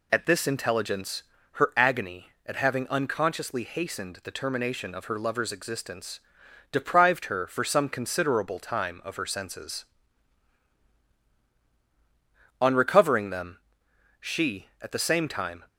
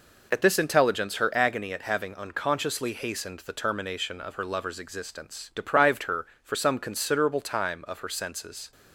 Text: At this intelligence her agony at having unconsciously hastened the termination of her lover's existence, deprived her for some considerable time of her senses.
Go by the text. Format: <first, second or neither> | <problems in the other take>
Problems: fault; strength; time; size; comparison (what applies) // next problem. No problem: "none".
second | pauses between "intelligence" and "her"; slight; at 1.2 s; 0.30 s long // goes on to say "On recovering them she at the same time"; strong; from 12.5 s on; 3.0 s long